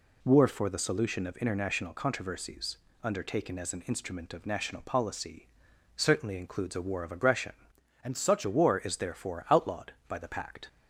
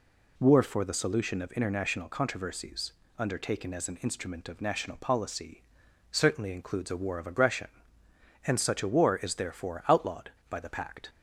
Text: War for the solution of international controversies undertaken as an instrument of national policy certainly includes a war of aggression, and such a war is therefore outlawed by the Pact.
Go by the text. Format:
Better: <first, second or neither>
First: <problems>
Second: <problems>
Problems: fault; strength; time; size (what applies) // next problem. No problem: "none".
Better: second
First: pauses between "controversies" and "undertaken"; slight; at 2.7 s; 0.26 s long // pauses between "policy" and "certainly"; noticeable; at 5.4 s; 0.50 s long // changes voice from "and" to "such"; from 8.0 to 8.4 s; 0.4 s long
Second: pauses between "controversies" and "undertaken"; slight; at 2.9 s; 0.26 s long // pauses between "policy" and "certainly"; noticeable; at 5.6 s; 0.50 s long